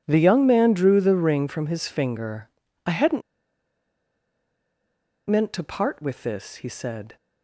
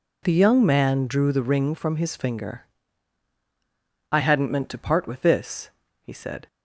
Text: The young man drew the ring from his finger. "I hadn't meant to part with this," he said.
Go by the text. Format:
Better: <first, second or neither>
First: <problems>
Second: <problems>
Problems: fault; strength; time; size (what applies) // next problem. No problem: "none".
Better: second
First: pauses between "hadn't" and "meant"; strong; at 3.2 s; 2.0 s long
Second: none